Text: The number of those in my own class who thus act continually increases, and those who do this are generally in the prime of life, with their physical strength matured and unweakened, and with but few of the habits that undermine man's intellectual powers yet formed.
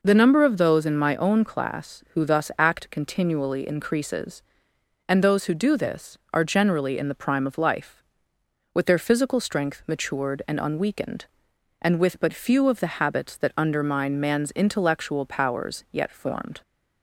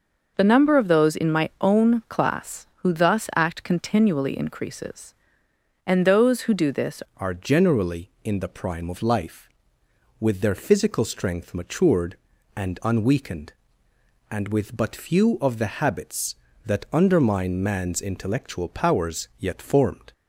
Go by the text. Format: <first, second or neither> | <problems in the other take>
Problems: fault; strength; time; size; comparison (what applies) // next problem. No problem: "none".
first | changes voice at "are"; from 7.1 s on; 13.0 s long